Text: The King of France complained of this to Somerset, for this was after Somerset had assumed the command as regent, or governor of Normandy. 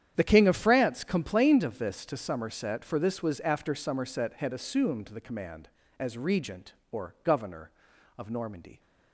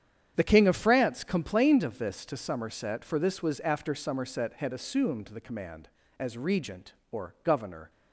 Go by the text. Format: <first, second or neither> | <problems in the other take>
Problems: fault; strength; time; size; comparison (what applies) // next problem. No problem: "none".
first | starts louder than the rest; strong; until 1.3 s; 9 dB; strong in the first // stops before "of Normandy"; at 7.8 s